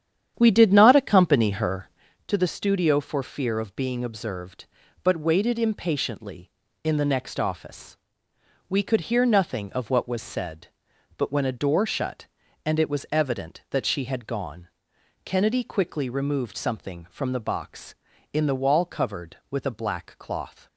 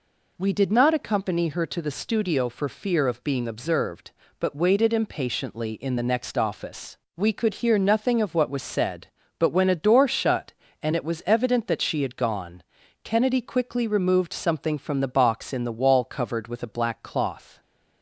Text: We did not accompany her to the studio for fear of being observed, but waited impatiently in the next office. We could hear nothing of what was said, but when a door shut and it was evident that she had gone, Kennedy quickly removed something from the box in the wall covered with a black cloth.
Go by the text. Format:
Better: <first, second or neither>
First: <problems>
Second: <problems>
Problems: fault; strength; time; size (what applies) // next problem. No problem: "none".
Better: second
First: starts louder than the rest; strong; until 2.1 s; 9.5 dB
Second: none